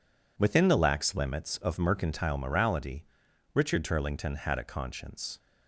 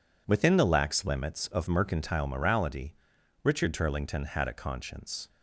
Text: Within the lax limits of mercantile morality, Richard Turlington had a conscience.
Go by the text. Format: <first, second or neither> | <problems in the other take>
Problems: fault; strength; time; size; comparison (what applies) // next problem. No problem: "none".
neither | none